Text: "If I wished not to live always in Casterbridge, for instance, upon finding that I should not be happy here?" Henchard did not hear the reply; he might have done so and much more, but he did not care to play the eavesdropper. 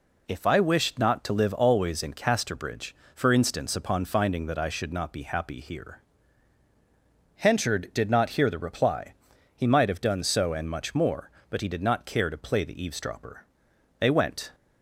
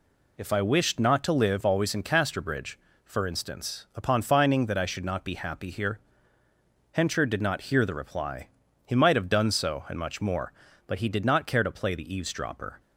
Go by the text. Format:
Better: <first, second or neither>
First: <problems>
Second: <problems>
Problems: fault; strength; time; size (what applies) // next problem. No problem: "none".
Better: second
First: goes on to say "They went"; from 13.9 s on; 0.54 s long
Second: none